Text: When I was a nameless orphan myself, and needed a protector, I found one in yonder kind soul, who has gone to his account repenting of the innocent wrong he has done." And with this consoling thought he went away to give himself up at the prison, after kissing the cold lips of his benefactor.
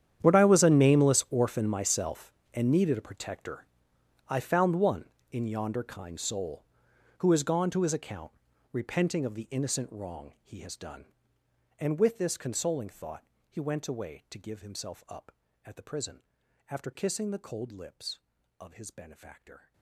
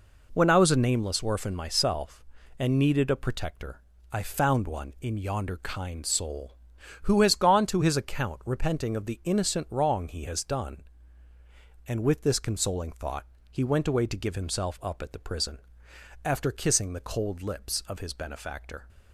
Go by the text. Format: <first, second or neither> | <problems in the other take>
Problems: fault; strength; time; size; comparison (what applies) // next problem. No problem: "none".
second | gets quieter; strong; throughout; 20.5 dB // pauses between "account" and "repenting"; at 8.3 s; 0.40 s long // pauses between "thought" and "he"; slight; at 13.2 s; 0.24 s long; slight in the second